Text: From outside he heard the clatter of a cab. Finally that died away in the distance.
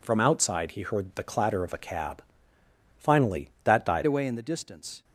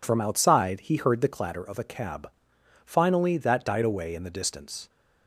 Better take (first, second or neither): second